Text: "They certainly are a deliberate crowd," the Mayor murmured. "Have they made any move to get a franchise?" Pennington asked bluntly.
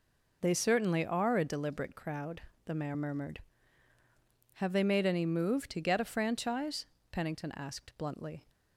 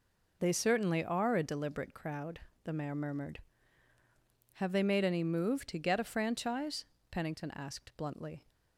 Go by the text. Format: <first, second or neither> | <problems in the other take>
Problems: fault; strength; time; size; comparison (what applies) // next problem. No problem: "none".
neither | none